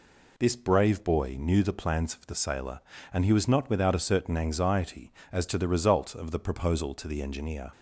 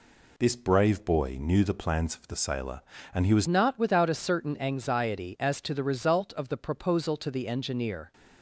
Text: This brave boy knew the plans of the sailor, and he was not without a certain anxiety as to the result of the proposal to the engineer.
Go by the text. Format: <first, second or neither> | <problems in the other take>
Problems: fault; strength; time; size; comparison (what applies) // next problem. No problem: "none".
first | changes voice at "not"; from 3.4 s on; 4.7 s long